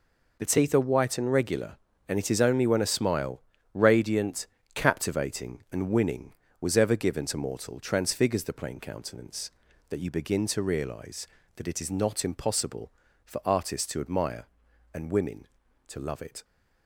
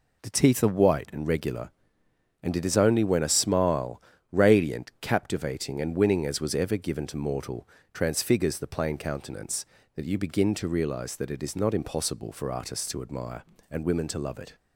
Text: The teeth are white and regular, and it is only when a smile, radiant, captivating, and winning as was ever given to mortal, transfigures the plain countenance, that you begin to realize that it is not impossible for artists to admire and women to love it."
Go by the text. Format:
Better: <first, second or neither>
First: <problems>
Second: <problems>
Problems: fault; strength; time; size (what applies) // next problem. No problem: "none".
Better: second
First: skips "as"; at 6.4 s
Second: none